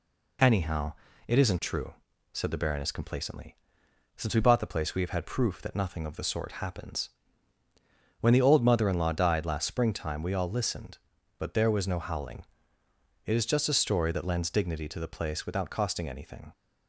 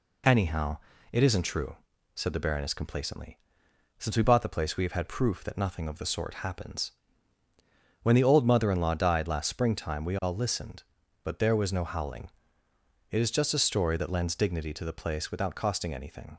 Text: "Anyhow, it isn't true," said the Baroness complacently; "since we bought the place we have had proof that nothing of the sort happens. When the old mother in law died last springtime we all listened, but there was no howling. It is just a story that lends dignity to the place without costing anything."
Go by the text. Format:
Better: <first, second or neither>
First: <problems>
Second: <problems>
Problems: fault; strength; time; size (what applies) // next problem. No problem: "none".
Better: neither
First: none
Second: none